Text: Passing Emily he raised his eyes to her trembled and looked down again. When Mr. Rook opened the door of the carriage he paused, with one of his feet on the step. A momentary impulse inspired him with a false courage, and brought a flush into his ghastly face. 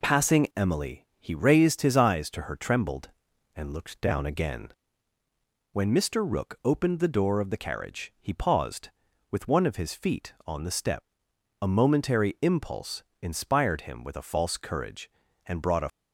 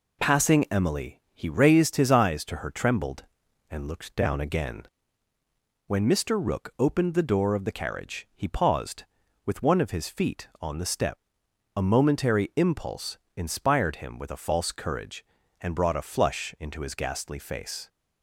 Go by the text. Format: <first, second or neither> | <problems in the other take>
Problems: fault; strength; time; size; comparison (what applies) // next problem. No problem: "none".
second | pauses between "impulse" and "inspired"; slight; at 13.0 s; 0.20 s long; slight in the second // stops before "flush into his ghastly face"; at 15.8 s